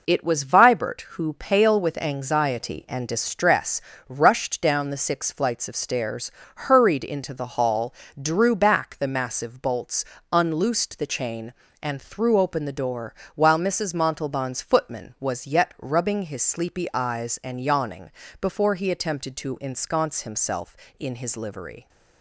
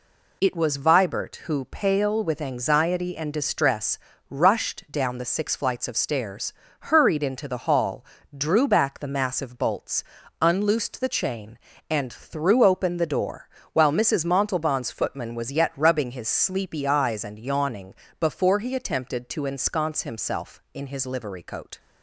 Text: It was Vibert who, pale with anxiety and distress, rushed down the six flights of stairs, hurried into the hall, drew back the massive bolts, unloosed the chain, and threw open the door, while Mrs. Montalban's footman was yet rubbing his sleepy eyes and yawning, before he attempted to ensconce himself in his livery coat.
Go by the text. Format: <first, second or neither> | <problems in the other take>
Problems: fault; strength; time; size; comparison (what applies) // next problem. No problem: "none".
second | stops before "coat"; at 21.8 s